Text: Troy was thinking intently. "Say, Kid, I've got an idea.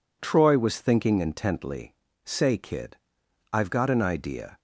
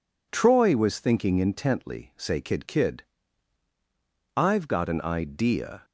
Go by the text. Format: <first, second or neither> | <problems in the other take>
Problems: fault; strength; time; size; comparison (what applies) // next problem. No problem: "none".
first | says "Kid" twice; at 2.6 s